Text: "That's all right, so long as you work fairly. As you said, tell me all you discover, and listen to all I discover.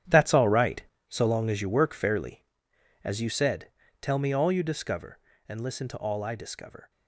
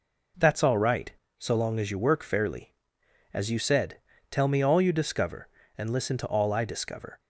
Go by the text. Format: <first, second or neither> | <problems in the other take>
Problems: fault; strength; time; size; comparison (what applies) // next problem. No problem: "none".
second | gets quieter; strong; throughout; 13 dB